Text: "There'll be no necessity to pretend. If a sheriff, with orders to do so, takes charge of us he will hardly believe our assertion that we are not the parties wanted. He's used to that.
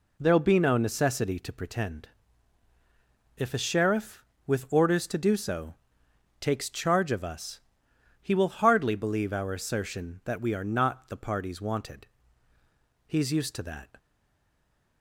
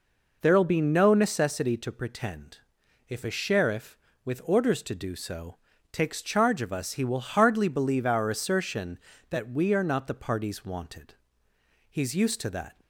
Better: second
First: pauses between "us" and "he"; noticeable; at 7.5 s; 0.60 s long // stays silent after the last word; from 13.9 s on; 1.1 s long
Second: none

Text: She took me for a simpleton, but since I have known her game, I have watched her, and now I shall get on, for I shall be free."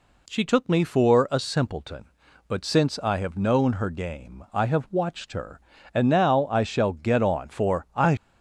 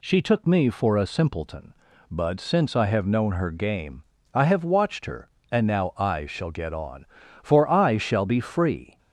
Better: second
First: stops before "shall be free"; at 8.1 s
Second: none

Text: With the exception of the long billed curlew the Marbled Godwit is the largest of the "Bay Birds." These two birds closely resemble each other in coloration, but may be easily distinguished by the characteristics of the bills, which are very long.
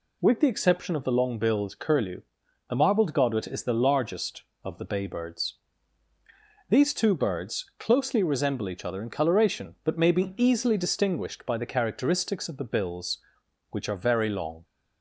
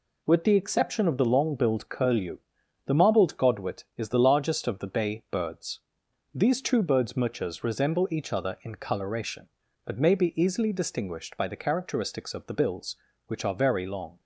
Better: first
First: pauses between "curlew" and "the"; noticeable; at 2.2 s; 0.48 s long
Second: pauses between "curlew" and "the"; noticeable; at 2.3 s; 0.48 s long // says "muchas" for "closely"; at 7.1 s

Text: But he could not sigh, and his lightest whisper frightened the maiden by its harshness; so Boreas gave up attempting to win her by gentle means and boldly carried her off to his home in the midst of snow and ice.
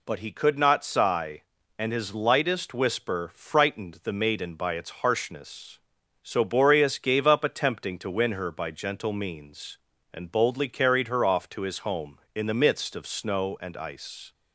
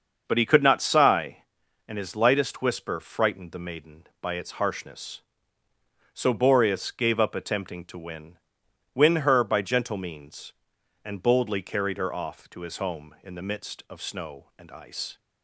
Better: first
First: none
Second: starts louder than the rest; until 1.2 s; 6.5 dB // says "win" twice; at 8.9 s

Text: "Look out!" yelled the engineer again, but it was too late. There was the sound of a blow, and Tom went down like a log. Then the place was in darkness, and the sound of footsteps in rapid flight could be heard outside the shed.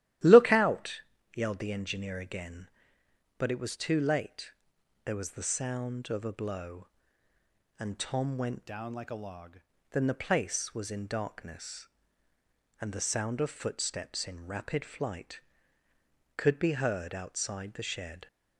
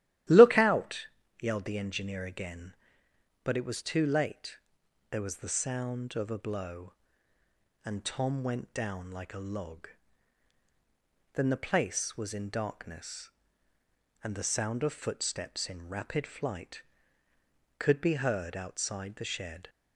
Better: second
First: starts louder than the rest; strong; until 1.5 s; 13.5 dB // changes voice from "down" to "log"; from 8.6 to 9.5 s; 0.9 s long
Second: starts louder than the rest; strong; until 1.6 s; 13.5 dB

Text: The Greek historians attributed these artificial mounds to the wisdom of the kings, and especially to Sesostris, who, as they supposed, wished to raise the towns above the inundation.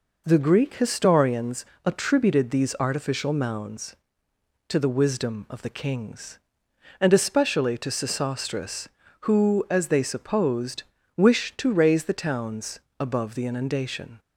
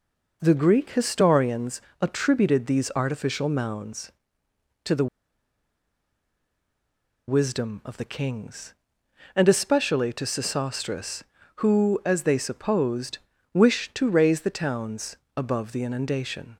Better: first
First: pauses between "historians" and "attributed"; slight; at 1.6 s; 0.22 s long // pauses between "towns" and "above"; slight; at 12.7 s; 0.18 s long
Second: pauses between "historians" and "attributed"; slight; at 1.7 s; 0.22 s long // pauses between "the" and "wisdom"; strong; at 5.0 s; 2.2 s long // pauses between "towns" and "above"; slight; at 15.1 s; 0.18 s long

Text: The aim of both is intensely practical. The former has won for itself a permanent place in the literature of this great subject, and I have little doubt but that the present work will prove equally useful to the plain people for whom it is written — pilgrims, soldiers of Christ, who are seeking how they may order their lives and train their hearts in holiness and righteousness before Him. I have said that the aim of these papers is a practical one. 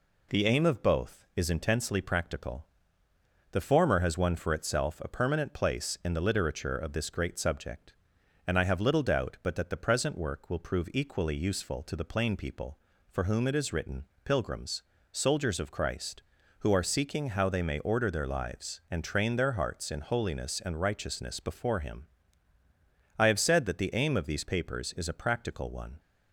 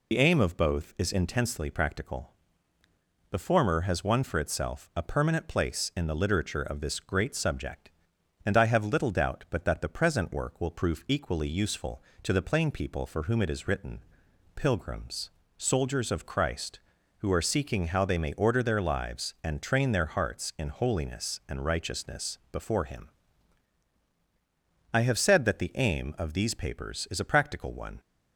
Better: first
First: none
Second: loses the start of "The"; at 0.1 s; 65 ms

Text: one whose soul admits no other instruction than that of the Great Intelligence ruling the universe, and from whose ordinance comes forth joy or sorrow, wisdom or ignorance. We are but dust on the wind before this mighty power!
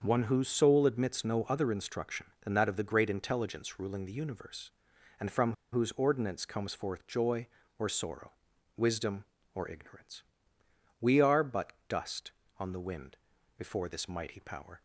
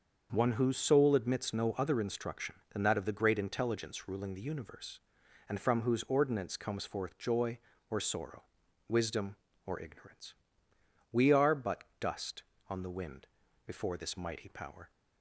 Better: second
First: starts louder than the rest; until 1.0 s; 6.5 dB // pauses between "from" and "whose"; slight; at 5.5 s; 0.20 s long // pauses between "but" and "dust"; slight; at 11.7 s; 0.16 s long // pauses between "wind" and "before"; at 13.1 s; 0.42 s long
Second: starts louder than the rest; until 1.3 s; 6.5 dB // pauses between "but" and "dust"; slight; at 11.8 s; 0.16 s long // pauses between "wind" and "before"; at 13.2 s; 0.40 s long

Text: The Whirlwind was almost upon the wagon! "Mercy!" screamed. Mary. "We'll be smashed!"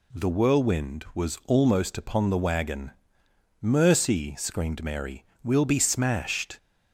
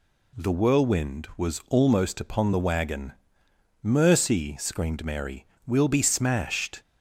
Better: neither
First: none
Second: none

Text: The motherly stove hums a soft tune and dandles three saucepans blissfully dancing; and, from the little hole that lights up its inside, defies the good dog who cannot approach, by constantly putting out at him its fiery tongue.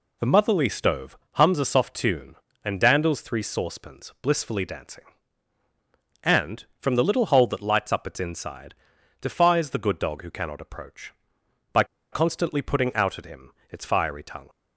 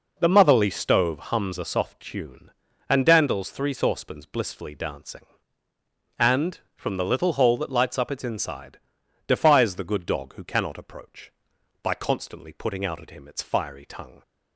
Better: second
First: pauses between "stove" and "hums"; slight; at 1.1 s; 0.16 s long // pauses between "by" and "constantly"; slight; at 11.8 s; 0.27 s long // pauses between "him" and "its"; slight; at 13.5 s; 0.18 s long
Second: none

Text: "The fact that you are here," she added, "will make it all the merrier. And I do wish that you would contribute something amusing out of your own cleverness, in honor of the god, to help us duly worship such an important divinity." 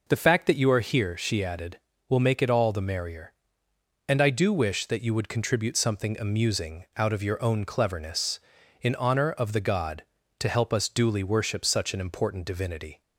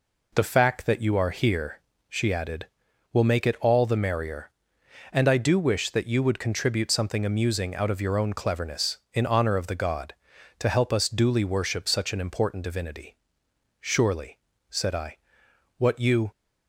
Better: first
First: none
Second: goes on to say "Surely said I what you"; strong; from 13.8 s on; 2.5 s long

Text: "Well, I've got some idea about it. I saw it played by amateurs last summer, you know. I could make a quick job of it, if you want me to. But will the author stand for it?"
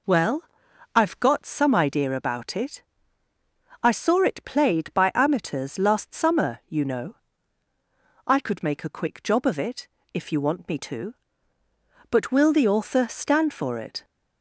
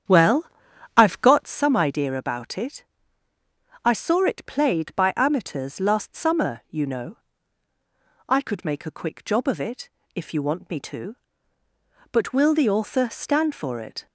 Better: first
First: none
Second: starts louder than the rest; strong; until 1.7 s; 8.5 dB

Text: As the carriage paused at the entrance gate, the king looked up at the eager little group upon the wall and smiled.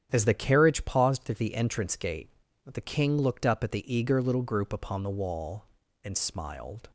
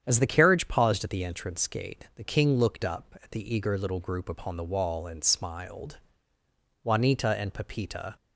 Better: first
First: starts louder than the rest; strong; until 1.1 s; 9 dB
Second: starts louder than the rest; strong; until 1.0 s; 9 dB // goes on to say "Juanita and Pepita"; from 6.8 s on; 1.3 s long

